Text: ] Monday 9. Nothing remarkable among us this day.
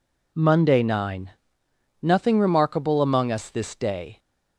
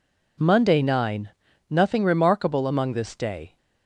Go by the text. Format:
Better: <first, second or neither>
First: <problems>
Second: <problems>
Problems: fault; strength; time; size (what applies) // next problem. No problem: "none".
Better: first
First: none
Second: skips "us"; at 2.9 s